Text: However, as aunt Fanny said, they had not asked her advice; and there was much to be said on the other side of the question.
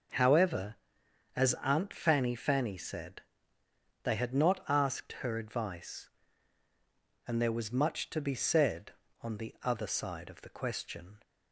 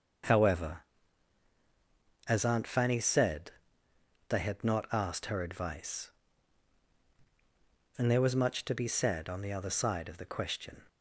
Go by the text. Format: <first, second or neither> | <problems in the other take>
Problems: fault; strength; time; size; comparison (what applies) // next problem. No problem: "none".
second | starts louder than the rest; noticeable; until 1.7 s; 6 dB // says "Fanny" twice; at 2.3 s